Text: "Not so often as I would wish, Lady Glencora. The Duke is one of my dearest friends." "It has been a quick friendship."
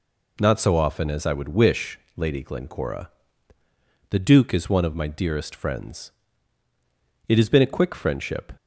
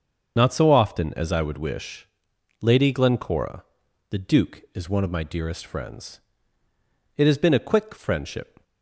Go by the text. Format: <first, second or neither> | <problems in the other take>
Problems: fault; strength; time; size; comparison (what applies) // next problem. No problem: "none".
first | loses the start of "Not"; at 0.3 s; 40 ms // starts louder than the rest; until 1.3 s; 7 dB